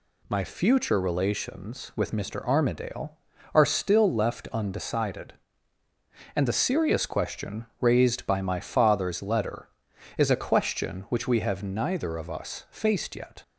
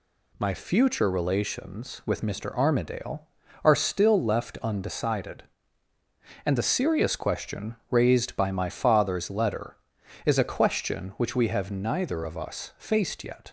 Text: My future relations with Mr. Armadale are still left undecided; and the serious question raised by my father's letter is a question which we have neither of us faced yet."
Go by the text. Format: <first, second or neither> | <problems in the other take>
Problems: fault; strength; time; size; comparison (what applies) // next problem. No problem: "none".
neither | pauses between "question" and "raised"; slight; the same in both